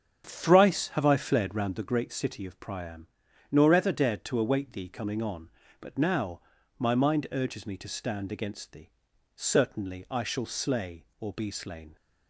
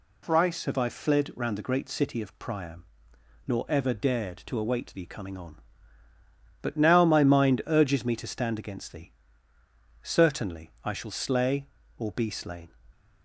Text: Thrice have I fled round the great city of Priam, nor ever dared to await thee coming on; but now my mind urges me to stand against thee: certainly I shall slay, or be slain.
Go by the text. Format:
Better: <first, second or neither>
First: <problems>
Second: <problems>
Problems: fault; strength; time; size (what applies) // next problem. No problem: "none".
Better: second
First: starts louder than the rest; strong; until 1.8 s; 8.5 dB // pauses between "now" and "my"; at 6.4 s; 0.38 s long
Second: none